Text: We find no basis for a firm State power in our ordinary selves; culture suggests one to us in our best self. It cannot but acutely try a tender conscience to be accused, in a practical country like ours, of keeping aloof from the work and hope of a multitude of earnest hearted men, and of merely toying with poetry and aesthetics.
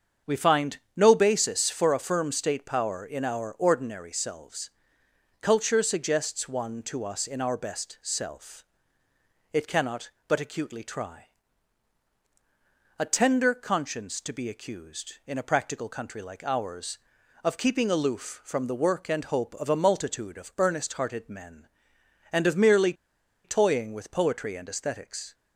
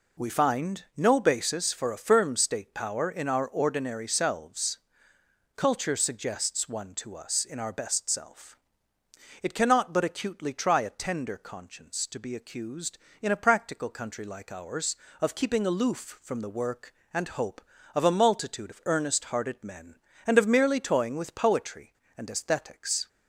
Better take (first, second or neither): second